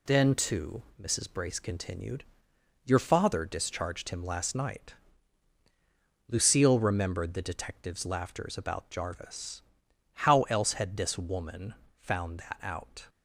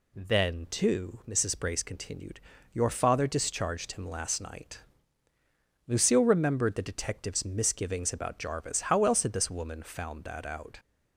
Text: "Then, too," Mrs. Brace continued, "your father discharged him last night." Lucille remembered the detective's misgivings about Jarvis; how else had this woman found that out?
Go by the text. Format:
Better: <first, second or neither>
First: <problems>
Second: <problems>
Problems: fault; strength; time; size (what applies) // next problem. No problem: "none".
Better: second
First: says "laughters" for "misgivings"; at 8.0 s // pauses between "woman" and "found"; slight; at 11.7 s; 0.24 s long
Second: none